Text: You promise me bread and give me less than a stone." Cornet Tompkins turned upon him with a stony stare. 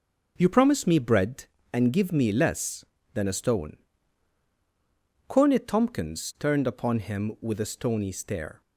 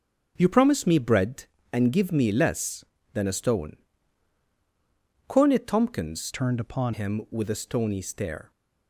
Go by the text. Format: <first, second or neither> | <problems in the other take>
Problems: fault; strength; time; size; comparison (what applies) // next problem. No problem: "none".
first | starts louder than the rest; strong; until 1.3 s; 7.5 dB; also in the first // changes voice from "turned" to "upon"; from 6.3 to 6.9 s; 0.6 s long